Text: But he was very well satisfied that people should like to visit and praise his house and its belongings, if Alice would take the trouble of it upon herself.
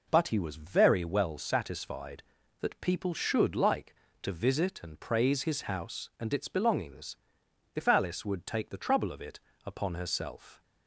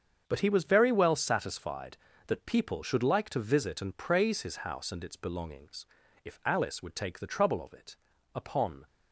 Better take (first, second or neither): first